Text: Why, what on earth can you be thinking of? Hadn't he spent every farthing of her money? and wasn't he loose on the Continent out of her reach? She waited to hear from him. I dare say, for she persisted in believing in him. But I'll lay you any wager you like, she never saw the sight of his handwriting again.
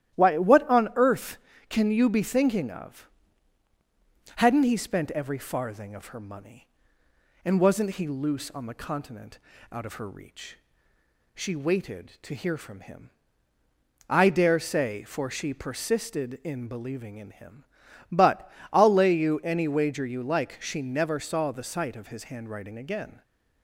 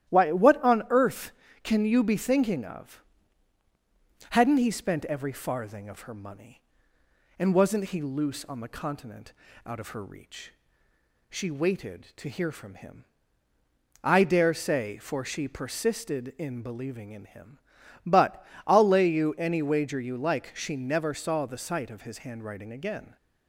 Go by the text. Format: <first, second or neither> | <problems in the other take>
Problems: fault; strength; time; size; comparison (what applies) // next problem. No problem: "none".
neither | starts louder than the rest; strong; the same in both // pauses between "Continent" and "out"; slight; the same in both // pauses between "But" and "I'll"; slight; the same in both